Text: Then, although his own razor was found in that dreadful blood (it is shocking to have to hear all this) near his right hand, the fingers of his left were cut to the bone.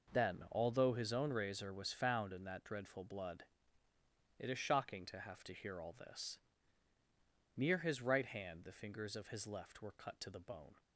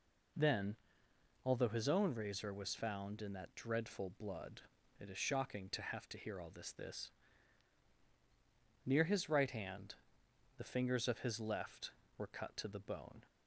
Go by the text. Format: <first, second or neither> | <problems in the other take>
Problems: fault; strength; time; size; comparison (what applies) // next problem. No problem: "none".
first | says "this" twice; at 6.7 s